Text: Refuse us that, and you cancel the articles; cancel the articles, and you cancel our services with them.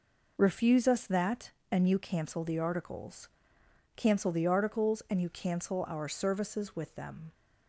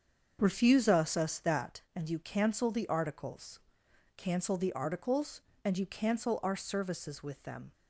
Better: first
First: none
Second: starts louder than the rest; until 1.4 s; 7 dB // says "us" twice; at 1.1 s

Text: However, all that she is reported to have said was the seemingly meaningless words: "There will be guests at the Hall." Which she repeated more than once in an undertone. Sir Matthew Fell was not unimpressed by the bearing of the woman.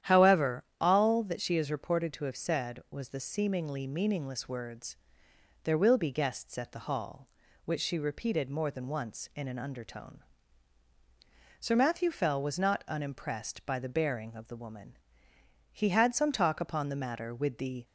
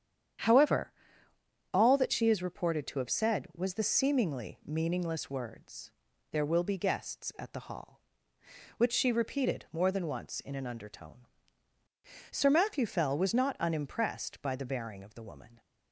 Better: second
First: starts louder than the rest; strong; until 1.1 s; 10.5 dB // goes on to say "He had some talk upon the matter with the"; strong; from 15.7 s on; 2.1 s long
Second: starts louder than the rest; strong; until 2.2 s; 9 dB

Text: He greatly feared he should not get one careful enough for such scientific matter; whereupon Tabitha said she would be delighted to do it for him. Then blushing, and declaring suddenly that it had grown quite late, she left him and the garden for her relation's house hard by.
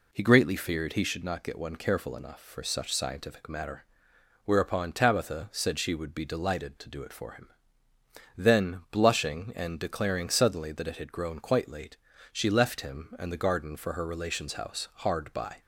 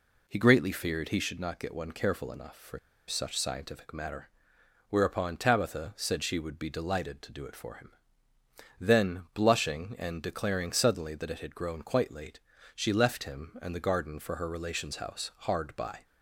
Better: first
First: none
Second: pauses between "for" and "such"; slight; at 2.7 s; 0.28 s long

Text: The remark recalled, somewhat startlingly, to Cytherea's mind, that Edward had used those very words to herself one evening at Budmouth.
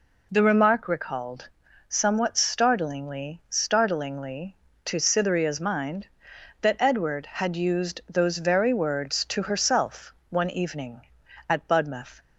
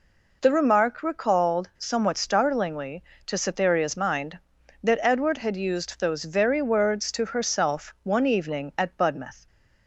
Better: second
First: says "startlingly" twice; at 3.4 s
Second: none

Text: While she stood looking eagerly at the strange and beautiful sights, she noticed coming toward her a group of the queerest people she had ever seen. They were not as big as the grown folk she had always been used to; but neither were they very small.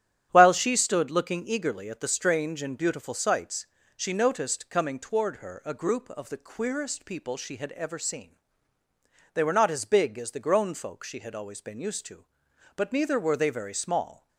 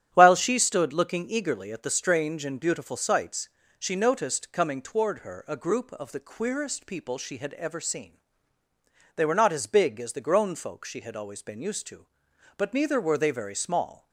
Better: neither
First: starts louder than the rest; strong; until 1.3 s; 10 dB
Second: starts louder than the rest; strong; until 1.1 s; 10 dB

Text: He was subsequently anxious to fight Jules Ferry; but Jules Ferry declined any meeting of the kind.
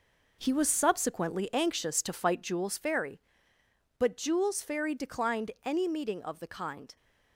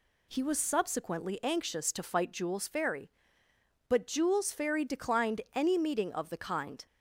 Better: second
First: gets quieter; strong; throughout; 9.5 dB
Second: none

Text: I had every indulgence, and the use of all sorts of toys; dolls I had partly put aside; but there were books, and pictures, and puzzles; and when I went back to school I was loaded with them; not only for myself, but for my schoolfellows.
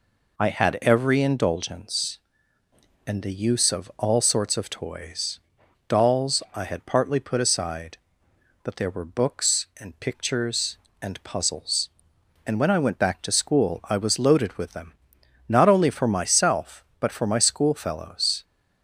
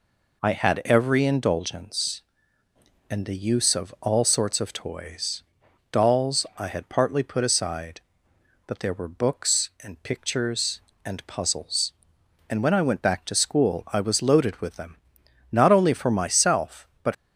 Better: first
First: none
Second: stops before "for my schoolfellows"; at 17.1 s

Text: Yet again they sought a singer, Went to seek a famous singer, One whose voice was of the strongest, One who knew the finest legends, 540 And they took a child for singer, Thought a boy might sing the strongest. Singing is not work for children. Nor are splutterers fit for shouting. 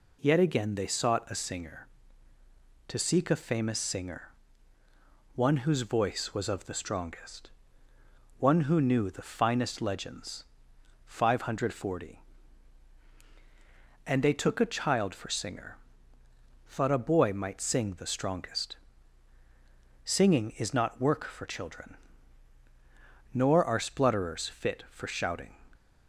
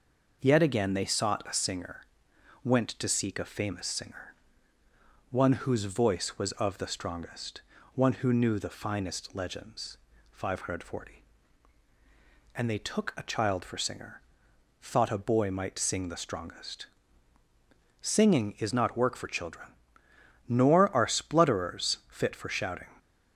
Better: second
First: skips "Went"; at 2.3 s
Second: none

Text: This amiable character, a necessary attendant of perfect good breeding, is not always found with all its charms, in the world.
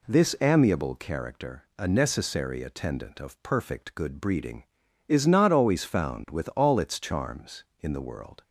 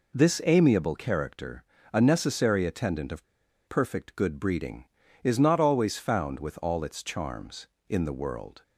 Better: first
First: none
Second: pauses between "of" and "perfect"; at 3.2 s; 0.43 s long

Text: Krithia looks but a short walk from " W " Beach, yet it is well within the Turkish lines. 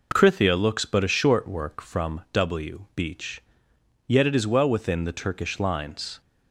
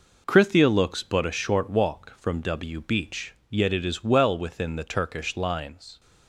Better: second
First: says "work" for "walk"; at 1.4 s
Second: none

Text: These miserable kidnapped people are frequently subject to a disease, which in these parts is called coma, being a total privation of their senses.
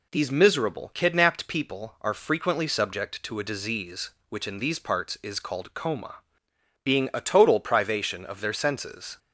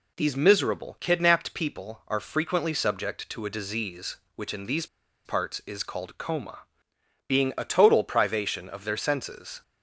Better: first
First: none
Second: pauses between "these" and "parts"; at 4.8 s; 0.39 s long

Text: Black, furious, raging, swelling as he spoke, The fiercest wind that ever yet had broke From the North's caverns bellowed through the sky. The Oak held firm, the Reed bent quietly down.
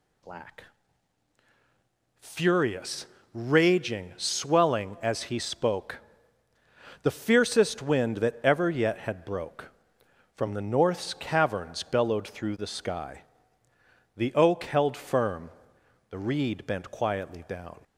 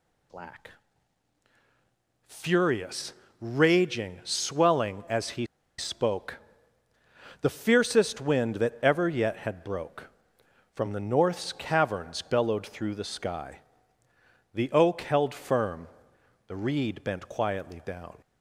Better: first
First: none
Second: pauses between "he" and "spoke"; slight; at 5.4 s; 0.33 s long

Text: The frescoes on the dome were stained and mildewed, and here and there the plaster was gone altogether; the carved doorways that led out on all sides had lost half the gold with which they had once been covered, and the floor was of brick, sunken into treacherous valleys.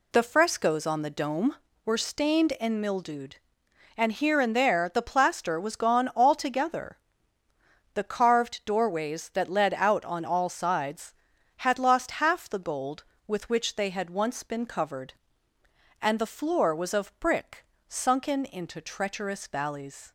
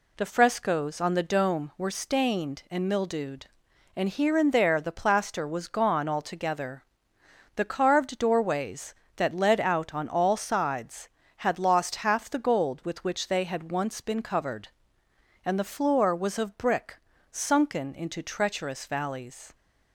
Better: neither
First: none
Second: none

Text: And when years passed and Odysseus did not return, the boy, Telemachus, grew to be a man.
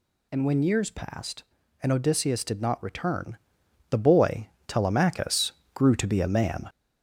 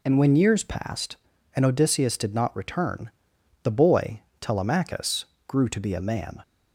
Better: second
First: gets louder; throughout; 3.5 dB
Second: none

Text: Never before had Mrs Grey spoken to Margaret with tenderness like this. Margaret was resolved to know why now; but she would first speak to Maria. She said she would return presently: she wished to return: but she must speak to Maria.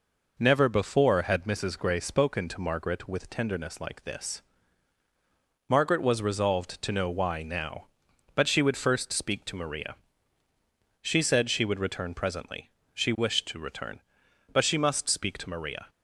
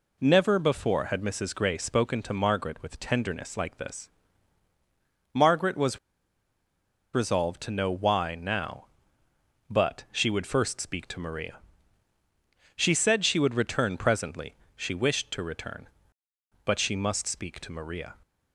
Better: first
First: none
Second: pauses between "was" and "resolved"; at 5.9 s; 1.1 s long

